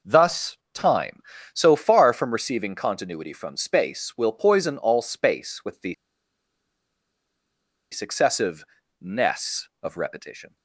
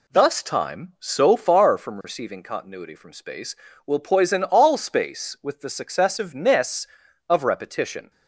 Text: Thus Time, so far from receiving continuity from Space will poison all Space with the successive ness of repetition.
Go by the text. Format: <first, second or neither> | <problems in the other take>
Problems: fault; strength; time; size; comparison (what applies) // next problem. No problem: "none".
second | pauses between "Thus" and "Time"; slight; at 0.5 s; 0.18 s long // pauses between "the" and "successive"; strong; at 5.9 s; 1.9 s long // pauses between "successive" and "ness"; slight; at 8.6 s; 0.34 s long